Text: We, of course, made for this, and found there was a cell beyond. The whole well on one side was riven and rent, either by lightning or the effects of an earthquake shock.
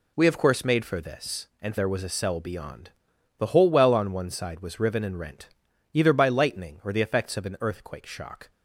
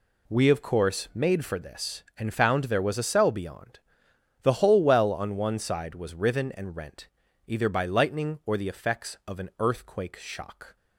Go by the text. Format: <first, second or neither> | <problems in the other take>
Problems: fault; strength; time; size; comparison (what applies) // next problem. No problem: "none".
second | skips "found"; at 1.7 s